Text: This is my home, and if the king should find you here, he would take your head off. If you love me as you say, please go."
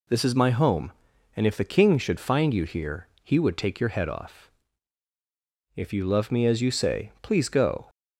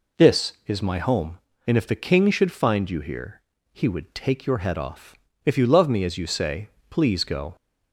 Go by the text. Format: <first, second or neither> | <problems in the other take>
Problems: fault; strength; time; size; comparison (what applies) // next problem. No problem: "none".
neither | none